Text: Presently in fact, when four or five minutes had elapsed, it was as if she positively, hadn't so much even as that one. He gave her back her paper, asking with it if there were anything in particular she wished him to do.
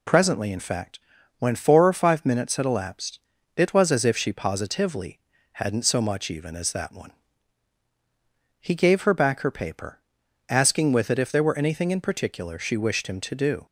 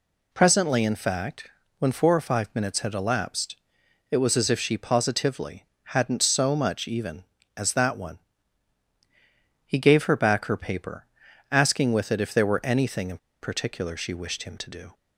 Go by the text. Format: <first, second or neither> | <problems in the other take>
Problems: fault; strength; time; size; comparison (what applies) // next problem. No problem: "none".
first | pauses between "in" and "particular"; slight; at 13.1 s; 0.23 s long